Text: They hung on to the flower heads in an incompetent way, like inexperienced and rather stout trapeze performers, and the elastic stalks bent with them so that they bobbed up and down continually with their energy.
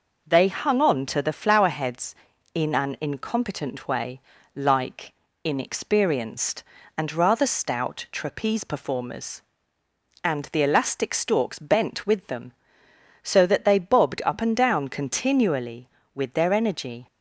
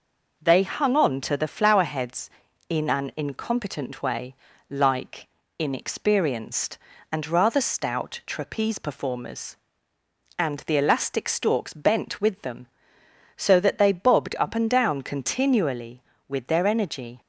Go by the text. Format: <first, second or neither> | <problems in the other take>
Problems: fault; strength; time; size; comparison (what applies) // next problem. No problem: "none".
neither | pauses between "like" and "inexperienced"; slight; the same in both